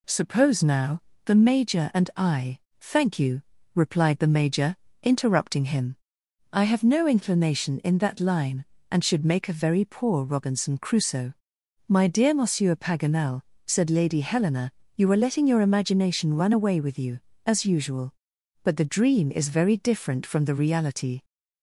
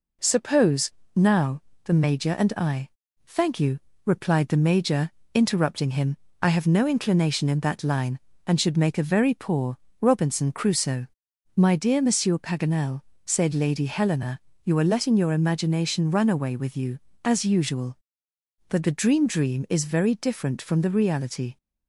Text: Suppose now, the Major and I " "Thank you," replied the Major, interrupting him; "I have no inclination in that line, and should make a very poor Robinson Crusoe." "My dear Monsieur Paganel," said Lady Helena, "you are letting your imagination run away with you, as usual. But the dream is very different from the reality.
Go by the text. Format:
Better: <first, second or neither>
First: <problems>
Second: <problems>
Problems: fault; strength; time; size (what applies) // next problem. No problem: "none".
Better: first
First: none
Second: pauses between "Suppose" and "now"; slight; at 0.9 s; 0.24 s long // pauses between "poor" and "Robinson"; slight; at 9.7 s; 0.24 s long // says "dream" twice; at 19.2 s